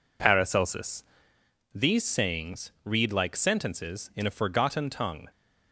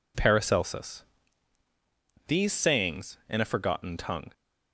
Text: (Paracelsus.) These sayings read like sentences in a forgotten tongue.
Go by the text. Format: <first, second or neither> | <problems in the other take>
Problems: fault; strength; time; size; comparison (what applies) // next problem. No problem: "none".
first | skips "read like sentences"; at 3.2 s